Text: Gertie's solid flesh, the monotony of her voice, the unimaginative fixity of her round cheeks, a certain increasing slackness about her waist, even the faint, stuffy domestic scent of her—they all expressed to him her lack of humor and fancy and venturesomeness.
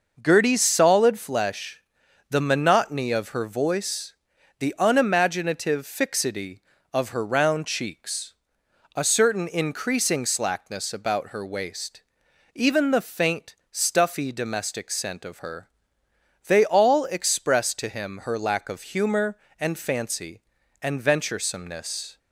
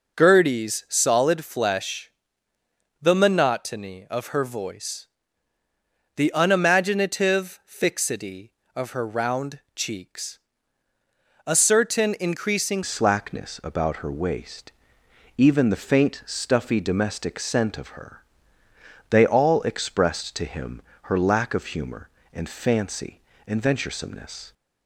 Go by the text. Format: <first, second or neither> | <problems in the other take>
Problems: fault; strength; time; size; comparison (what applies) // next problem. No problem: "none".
first | pauses between "round" and "cheeks"; slight; at 9.5 s; 0.16 s long // changes voice at "slackness"; from 12.8 s on; 11.7 s long // pauses between "him" and "her"; slight; at 20.8 s; 0.22 s long